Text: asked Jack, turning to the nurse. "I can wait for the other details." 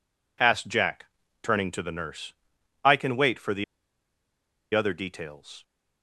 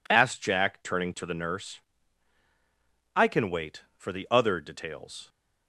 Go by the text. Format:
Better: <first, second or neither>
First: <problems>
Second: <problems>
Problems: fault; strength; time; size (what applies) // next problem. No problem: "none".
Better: second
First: pauses between "the" and "other"; at 3.6 s; 1.1 s long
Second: none